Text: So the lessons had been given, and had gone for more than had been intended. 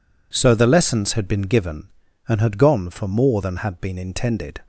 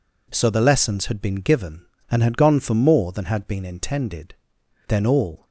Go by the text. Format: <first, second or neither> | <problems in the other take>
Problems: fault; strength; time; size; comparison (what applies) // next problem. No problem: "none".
first | goes on to say "Then all"; from 4.8 s on; 0.58 s long